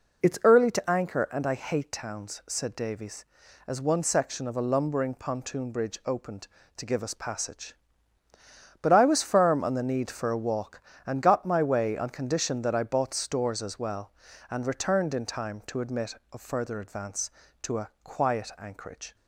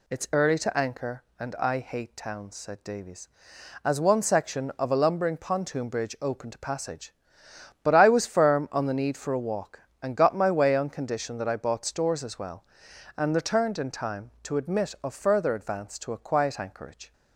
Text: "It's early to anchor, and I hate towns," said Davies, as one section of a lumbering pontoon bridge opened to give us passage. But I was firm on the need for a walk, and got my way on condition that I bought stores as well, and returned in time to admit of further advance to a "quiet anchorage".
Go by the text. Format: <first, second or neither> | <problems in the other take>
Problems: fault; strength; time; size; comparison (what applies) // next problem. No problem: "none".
first | skips "give us"; at 6.5 s